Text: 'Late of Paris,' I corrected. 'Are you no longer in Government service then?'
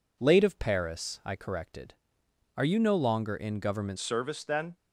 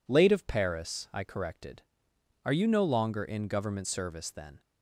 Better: second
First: changes voice at "service"; from 3.9 s on; 0.8 s long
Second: none

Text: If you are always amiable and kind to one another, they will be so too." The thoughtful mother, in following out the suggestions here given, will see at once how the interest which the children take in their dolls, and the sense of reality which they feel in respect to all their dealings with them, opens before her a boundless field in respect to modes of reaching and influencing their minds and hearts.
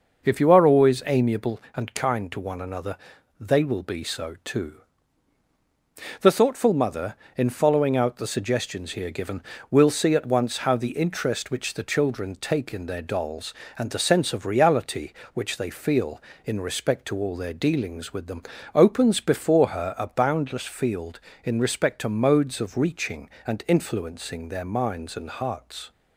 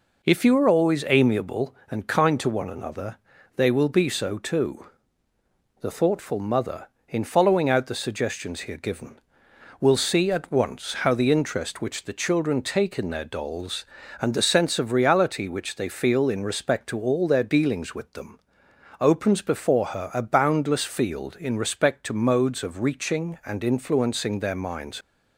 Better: first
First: none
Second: stops before "and hearts"; at 25.0 s

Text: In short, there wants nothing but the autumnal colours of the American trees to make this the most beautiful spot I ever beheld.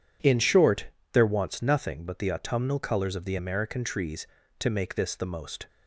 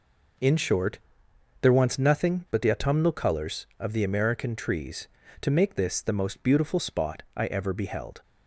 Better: second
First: stops before "beautiful spot I ever beheld"; at 5.6 s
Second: none

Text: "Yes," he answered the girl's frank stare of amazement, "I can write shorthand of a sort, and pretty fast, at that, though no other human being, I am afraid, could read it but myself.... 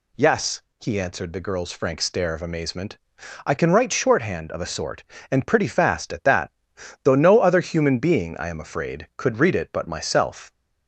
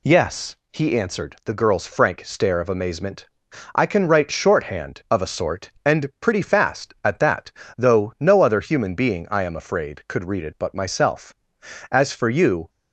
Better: first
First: none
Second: goes on to say "As for you"; noticeable; from 11.8 s on; 0.80 s long

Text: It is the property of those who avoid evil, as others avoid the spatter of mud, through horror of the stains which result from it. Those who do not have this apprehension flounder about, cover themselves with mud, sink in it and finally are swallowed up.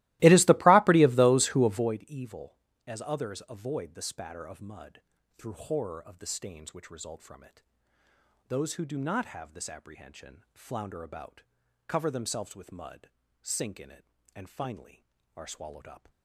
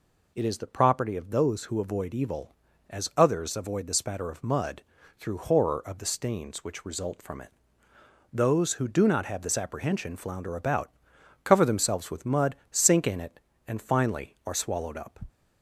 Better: second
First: starts louder than the rest; strong; until 2.0 s; 18.5 dB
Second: none

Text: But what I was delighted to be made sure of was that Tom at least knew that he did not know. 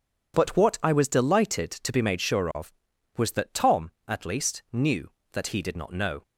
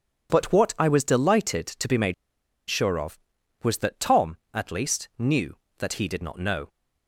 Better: first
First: none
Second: pauses between "made" and "sure"; noticeable; at 2.1 s; 0.54 s long

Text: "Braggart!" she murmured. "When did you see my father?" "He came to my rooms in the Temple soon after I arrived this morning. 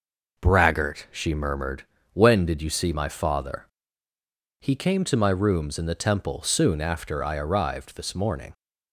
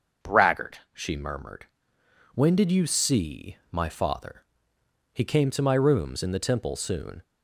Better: first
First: none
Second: starts louder than the rest; until 1.3 s; 6 dB // stops before "after I arrived this morning"; at 7.2 s

